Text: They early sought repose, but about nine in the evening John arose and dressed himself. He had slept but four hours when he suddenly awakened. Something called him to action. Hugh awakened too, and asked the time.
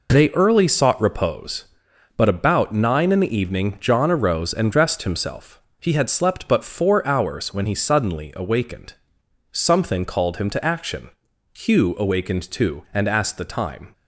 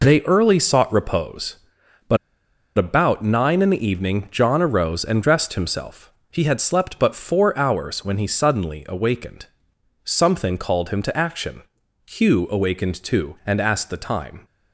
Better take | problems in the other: first | pauses between "but" and "about"; noticeable; at 2.1 s; 0.59 s long

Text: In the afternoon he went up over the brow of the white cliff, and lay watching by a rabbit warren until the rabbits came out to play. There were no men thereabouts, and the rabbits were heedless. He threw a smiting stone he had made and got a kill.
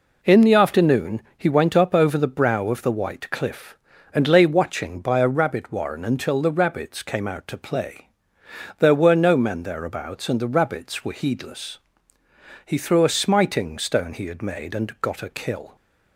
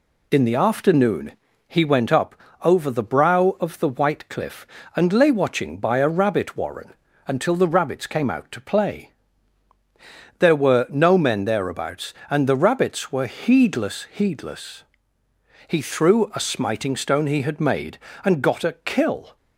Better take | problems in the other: first | pauses between "afternoon" and "he"; slight; at 1.3 s; 0.36 s long // pauses between "up" and "over"; slight; at 2.3 s; 0.30 s long // pauses between "warren" and "until"; slight; at 6.9 s; 0.34 s long // says "heedless" twice; at 14.1 s

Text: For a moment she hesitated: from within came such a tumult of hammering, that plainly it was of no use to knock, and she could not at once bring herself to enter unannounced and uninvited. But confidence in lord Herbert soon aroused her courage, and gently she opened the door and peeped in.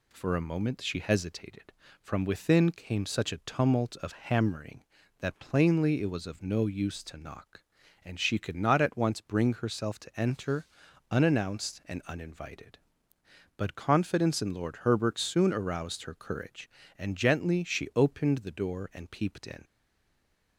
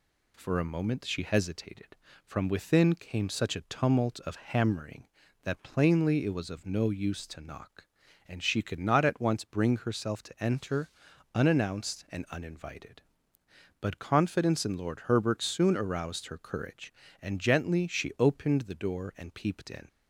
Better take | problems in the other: second | pauses between "enter" and "unannounced"; at 10.6 s; 0.44 s long; also in the second // stays silent after the last word; slight; from 19.6 s on; 0.9 s long

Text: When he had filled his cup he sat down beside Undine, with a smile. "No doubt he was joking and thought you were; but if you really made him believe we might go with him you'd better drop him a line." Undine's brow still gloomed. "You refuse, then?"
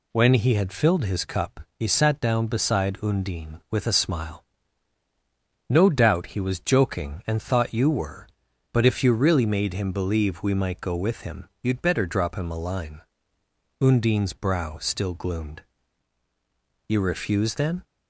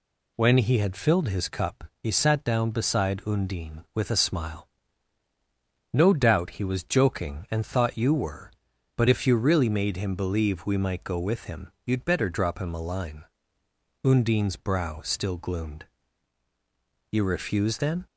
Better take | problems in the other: neither | pauses between "cup" and "he"; slight; the same in both

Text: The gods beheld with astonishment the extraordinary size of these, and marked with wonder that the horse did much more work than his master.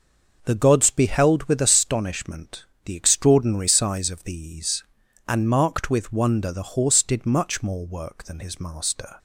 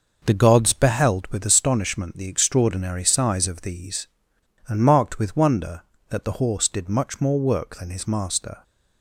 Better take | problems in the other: second | pauses between "astonishment" and "the"; slight; at 2.6 s; 0.20 s long // skips "that"; at 6.5 s

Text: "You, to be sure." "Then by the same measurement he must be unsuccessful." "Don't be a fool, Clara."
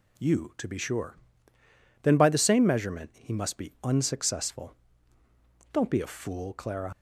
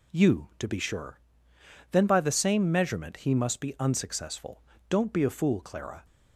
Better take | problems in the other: second | leaves "Clara" unfinished; at 6.9 s; 65 ms

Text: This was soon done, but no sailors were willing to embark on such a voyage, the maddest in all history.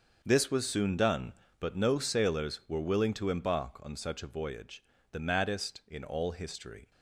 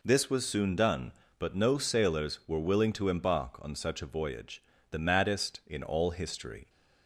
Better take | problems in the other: second | gets quieter; strong; throughout; 13.5 dB

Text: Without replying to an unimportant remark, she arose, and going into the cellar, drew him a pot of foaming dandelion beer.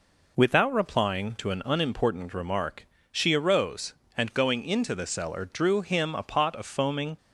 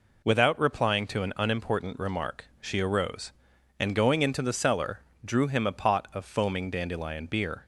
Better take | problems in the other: second | stops before "dandelion beer"; at 7.1 s

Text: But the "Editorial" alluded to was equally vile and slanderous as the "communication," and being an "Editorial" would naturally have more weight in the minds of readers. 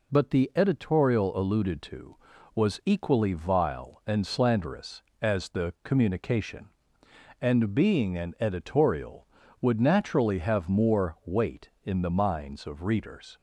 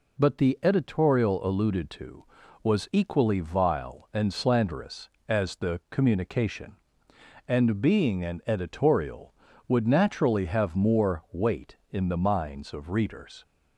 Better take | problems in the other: neither | none

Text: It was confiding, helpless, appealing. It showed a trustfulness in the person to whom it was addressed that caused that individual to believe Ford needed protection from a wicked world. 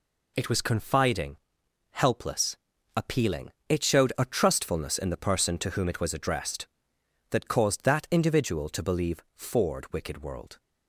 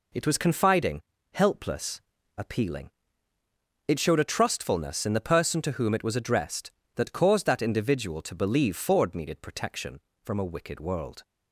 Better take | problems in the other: second | skips "needed protection from a"; at 9.9 s

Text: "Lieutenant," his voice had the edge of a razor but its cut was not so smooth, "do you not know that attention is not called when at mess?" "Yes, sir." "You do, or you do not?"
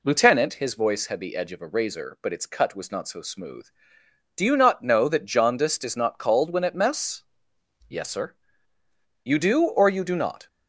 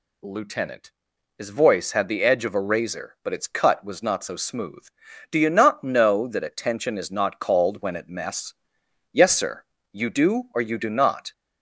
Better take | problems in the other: second | says "jaundiced" for "attention"; at 5.2 s

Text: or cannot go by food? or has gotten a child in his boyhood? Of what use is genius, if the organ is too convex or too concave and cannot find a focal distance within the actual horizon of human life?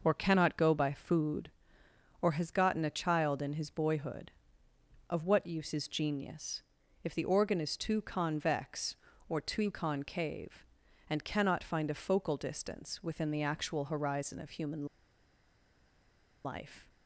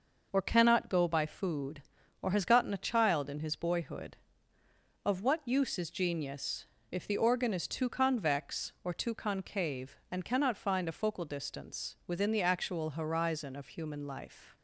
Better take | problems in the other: second | pauses between "human" and "life"; strong; at 14.8 s; 1.5 s long

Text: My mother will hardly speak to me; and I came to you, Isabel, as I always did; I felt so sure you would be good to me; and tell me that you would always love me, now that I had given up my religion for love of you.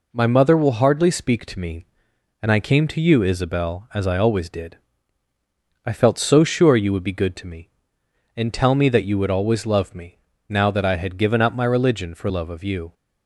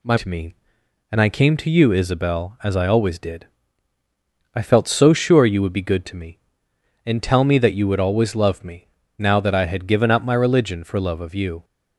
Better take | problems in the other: first | skips "mother will hardly speak"; at 0.1 s

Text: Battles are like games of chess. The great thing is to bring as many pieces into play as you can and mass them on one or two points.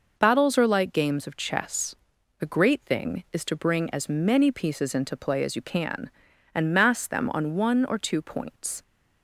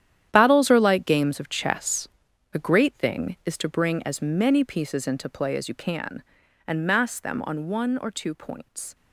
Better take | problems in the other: first | gets quieter; strong; throughout; 13 dB

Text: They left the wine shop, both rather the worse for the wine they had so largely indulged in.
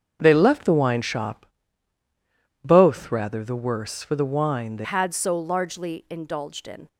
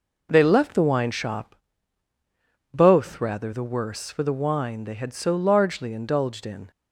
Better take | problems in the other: second | starts louder than the rest; strong; until 1.2 s; 7 dB // changes voice at "had"; from 4.8 s on; 2.0 s long

